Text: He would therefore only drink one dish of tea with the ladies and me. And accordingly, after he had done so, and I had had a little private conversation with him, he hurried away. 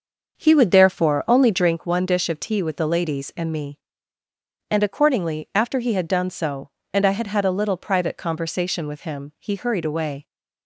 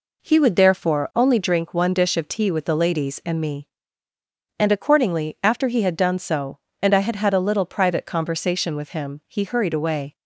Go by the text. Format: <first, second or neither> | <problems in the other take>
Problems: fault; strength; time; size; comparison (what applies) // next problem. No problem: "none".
second | starts louder than the rest; until 1.9 s; 6 dB